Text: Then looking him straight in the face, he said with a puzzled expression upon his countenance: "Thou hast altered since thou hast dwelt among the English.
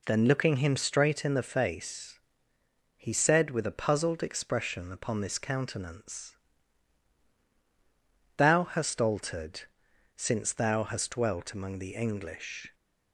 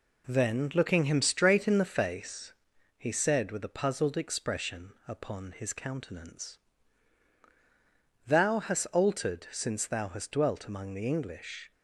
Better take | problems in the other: second | says "this" for "his"; at 5.2 s // pauses between "altered" and "since"; noticeable; at 9.6 s; 0.52 s long

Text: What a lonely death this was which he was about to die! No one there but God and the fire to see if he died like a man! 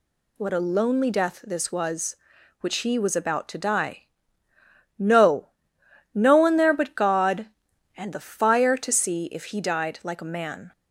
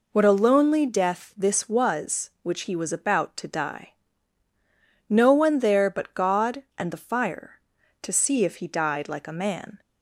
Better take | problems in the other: second | says "No" twice; at 6.1 s

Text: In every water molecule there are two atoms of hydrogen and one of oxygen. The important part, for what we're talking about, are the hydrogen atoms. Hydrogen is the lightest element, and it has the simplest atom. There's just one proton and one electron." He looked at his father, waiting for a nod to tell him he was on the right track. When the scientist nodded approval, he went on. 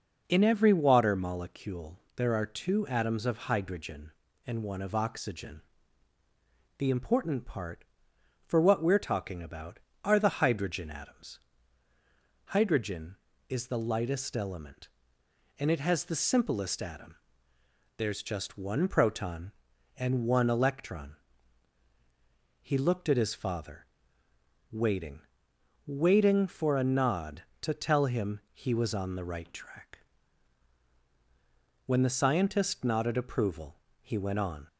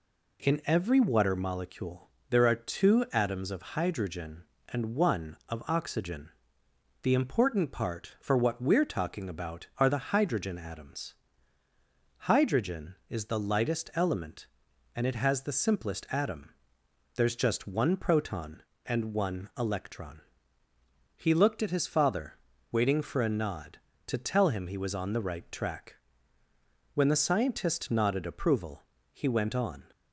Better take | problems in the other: second | pauses between "molecule" and "there"; slight; at 1.9 s; 0.16 s long; slight in the second // says "waiting" twice; at 25.8 s // pauses between "him" and "he"; slight; at 28.3 s; 0.16 s long

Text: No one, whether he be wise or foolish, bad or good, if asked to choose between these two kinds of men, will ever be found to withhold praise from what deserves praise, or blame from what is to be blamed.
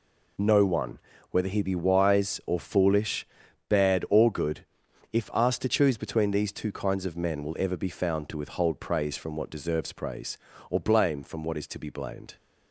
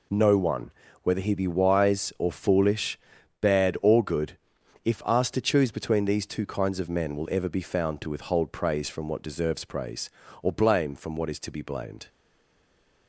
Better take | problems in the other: first | stays silent after the last word; from 12.0 s on; 1.0 s long

